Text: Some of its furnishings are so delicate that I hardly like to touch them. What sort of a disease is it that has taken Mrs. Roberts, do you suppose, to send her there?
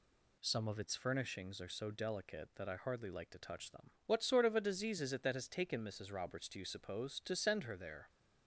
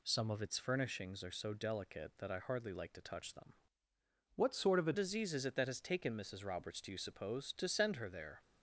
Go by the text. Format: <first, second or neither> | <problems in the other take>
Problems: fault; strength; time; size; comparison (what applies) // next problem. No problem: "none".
first | changes voice from "What" to "a"; from 4.3 to 4.9 s; 0.6 s long